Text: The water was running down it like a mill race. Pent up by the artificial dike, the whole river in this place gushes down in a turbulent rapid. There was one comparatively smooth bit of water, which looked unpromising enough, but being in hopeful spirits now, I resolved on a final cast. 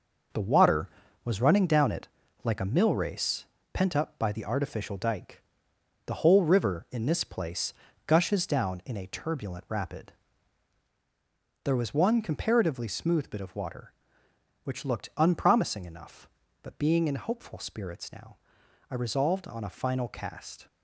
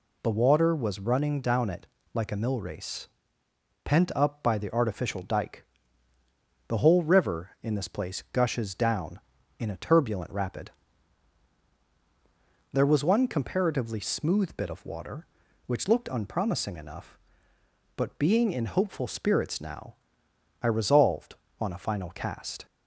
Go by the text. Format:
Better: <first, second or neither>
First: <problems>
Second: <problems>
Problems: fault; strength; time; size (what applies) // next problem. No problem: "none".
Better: second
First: gets quieter; strong; throughout; 7.5 dB // pauses between "it" and "like"; at 2.0 s; 0.38 s long // pauses between "place" and "gushes"; slight; at 7.7 s; 0.34 s long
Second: pauses between "it" and "like"; slight; at 1.8 s; 0.26 s long